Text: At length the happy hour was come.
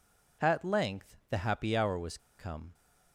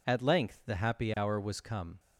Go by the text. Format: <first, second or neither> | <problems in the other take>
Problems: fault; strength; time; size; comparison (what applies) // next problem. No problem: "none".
second | pauses between "was" and "come"; slight; at 2.1 s; 0.20 s long